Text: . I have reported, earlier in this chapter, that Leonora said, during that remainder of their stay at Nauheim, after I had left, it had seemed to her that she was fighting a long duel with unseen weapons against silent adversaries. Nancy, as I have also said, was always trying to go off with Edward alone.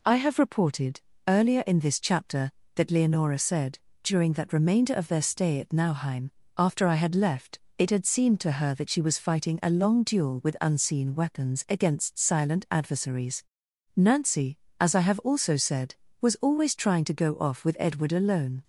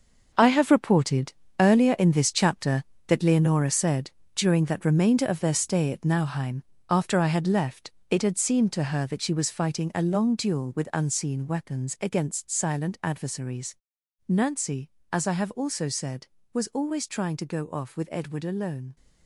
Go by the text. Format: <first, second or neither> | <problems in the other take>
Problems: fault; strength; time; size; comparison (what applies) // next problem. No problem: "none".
first | gets quieter; strong; throughout; 10 dB